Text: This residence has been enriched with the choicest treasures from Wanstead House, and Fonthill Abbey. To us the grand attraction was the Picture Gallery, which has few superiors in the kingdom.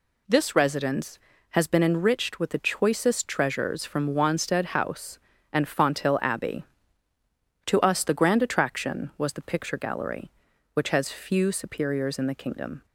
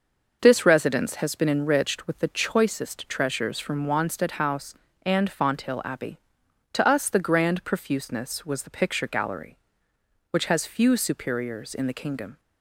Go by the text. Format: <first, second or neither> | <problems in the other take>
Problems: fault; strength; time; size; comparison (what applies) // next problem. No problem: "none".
first | says "profuseness" for "attraction"; at 7.6 s